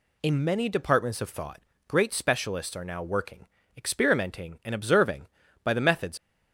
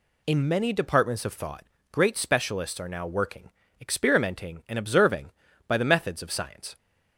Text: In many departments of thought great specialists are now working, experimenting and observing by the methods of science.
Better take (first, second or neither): second